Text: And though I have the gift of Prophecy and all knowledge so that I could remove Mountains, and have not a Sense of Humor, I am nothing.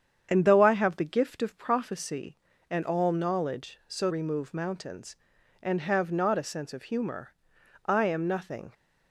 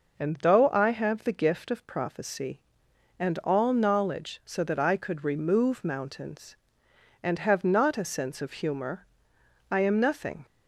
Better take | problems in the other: second | starts louder than the rest; strong; until 1.3 s; 8 dB // skips "that I could"; at 4.1 s

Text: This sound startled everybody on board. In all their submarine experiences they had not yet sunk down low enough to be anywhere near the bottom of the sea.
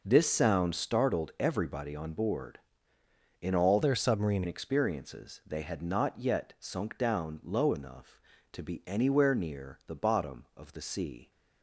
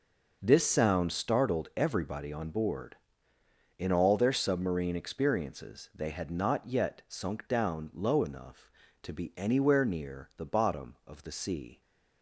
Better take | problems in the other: second | changes voice from "their" to "submarine"; from 3.8 to 4.4 s; 0.6 s long

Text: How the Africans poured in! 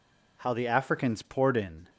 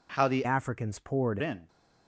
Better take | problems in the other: first | changes voice from "Africans" to "poured"; from 0.4 to 1.3 s; 0.9 s long

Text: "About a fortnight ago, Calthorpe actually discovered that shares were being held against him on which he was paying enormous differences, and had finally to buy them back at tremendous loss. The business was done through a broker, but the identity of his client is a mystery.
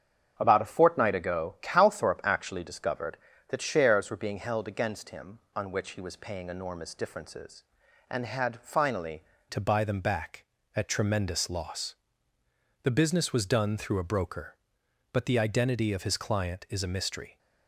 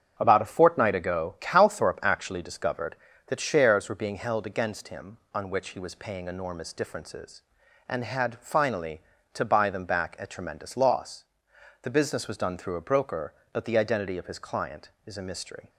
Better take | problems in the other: second | starts louder than the rest; strong; until 1.3 s; 8 dB; strong in the second // changes voice at "to"; from 9.4 s on; 7.9 s long

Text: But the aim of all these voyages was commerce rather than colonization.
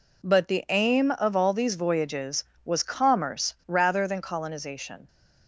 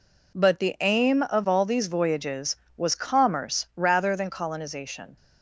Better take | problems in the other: neither | none

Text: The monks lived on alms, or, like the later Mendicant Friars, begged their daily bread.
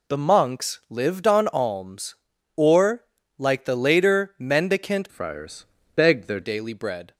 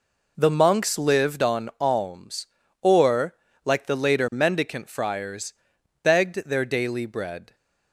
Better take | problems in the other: second | changes voice from "Friars" to "their"; from 5.0 to 6.4 s; 1.4 s long

